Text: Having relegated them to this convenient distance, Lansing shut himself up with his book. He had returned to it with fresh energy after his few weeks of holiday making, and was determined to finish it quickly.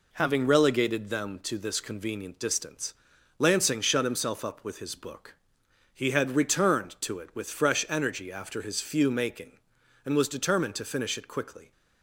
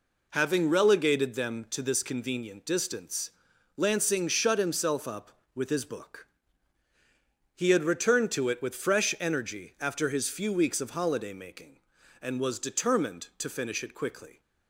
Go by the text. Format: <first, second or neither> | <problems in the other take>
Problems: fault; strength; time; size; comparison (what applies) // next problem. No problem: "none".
second | skips "weeks of holiday"; at 9.0 s